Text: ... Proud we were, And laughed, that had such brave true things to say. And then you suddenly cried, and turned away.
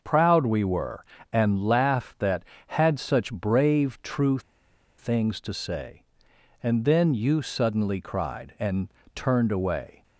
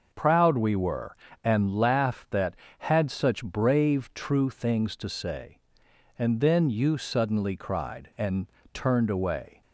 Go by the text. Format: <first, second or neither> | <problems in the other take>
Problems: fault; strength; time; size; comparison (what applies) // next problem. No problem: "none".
second | pauses between "true" and "things"; noticeable; at 4.3 s; 0.58 s long // pauses between "and" and "turned"; slight; at 8.8 s; 0.26 s long; slight in the second